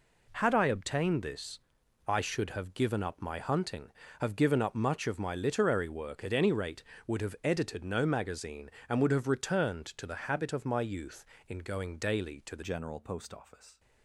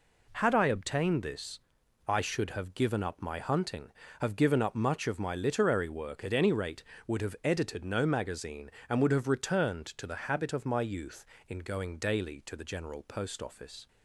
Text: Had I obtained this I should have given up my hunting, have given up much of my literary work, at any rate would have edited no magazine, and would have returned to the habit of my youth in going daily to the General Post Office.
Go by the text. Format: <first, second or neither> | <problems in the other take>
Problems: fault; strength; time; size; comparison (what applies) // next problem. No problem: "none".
second | pauses between "this" and "I"; noticeable; at 1.5 s; 0.48 s long; noticeable in the second // changes voice at "General"; from 12.6 s on; 1.1 s long